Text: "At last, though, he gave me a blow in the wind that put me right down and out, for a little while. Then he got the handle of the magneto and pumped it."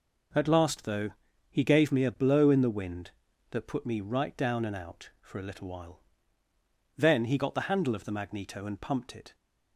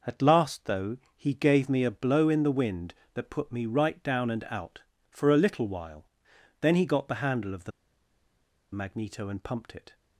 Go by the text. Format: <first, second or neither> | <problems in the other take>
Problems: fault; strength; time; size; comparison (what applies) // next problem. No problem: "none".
first | pauses between "the" and "magneto"; at 7.7 s; 1.0 s long